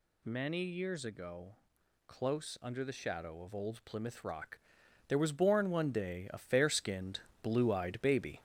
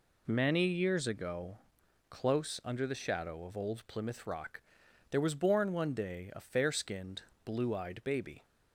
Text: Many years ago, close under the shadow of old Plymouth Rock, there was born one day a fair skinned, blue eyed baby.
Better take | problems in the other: second | gets louder; noticeable; throughout; 4.5 dB

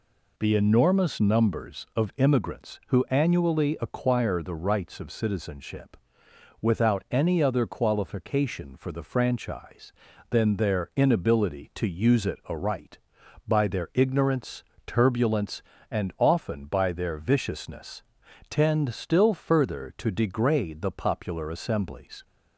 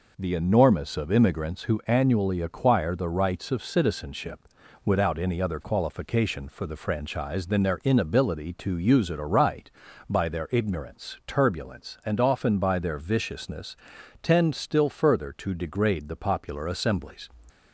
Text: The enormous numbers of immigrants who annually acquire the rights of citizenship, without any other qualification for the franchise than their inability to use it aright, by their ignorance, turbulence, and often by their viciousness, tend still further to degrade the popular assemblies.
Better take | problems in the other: first | skips "numbers"; at 0.9 s

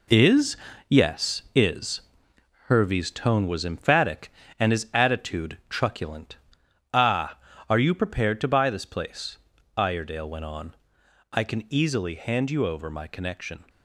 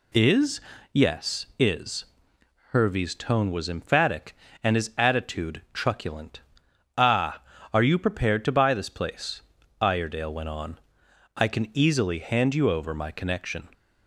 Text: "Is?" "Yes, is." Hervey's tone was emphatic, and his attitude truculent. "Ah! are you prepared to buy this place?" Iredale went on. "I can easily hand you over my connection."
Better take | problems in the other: second | gets quieter; strong; throughout; 8 dB

